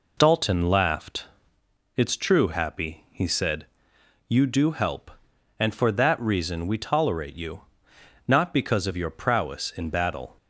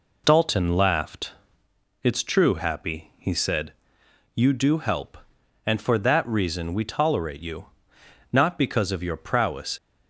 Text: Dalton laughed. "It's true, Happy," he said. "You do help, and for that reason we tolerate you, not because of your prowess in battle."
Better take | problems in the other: first | stops before "in battle"; at 9.7 s

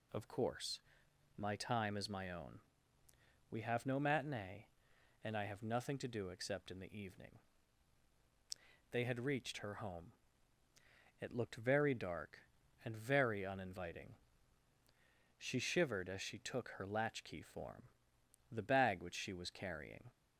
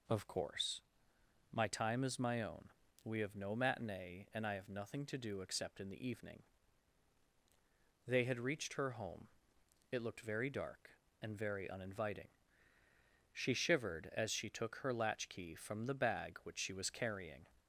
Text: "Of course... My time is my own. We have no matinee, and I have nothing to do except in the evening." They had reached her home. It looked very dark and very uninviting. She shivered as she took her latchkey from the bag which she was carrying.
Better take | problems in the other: second | says "form" for "from"; at 17.4 s

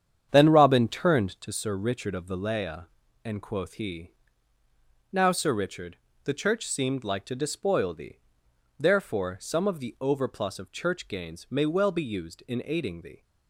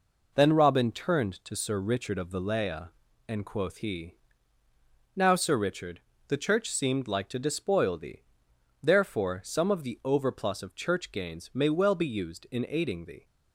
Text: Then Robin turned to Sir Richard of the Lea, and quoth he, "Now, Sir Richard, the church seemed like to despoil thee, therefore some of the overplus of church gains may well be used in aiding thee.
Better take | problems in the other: second | starts louder than the rest; strong; until 1.6 s; 8.5 dB

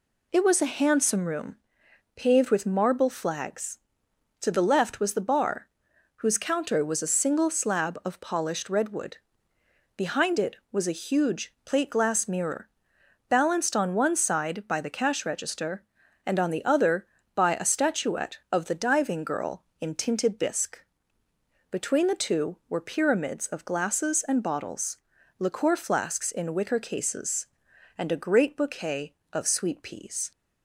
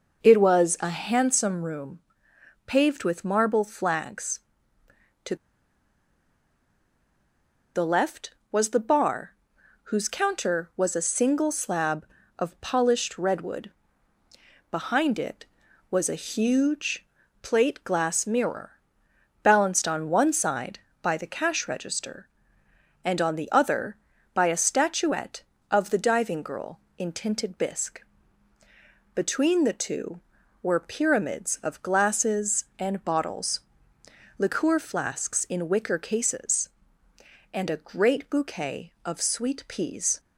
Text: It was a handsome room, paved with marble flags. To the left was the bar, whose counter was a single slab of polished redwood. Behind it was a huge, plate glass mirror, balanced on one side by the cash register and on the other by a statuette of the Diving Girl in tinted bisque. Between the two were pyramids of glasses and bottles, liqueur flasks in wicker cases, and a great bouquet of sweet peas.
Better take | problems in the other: first | pauses between "To" and "the"; strong; at 5.3 s; 2.4 s long

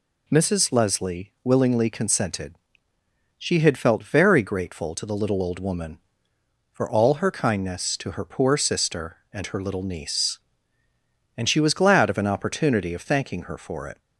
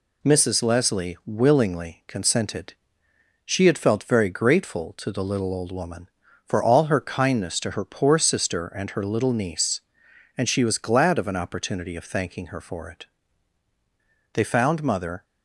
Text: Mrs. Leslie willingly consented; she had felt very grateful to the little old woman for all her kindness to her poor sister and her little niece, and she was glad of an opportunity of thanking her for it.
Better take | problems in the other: first | goes on to say "They found Mother"; noticeable; from 14.3 s on; 0.90 s long

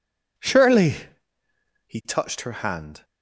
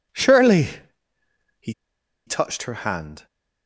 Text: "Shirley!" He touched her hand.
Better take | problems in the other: first | pauses between "He" and "touched"; noticeable; at 1.7 s; 0.55 s long

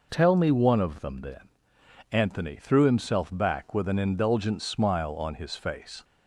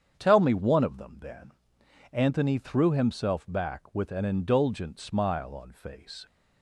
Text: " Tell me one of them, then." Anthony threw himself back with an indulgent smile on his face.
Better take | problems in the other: first | starts louder than the rest; strong; until 1.1 s; 8 dB // skips "his"; at 5.7 s

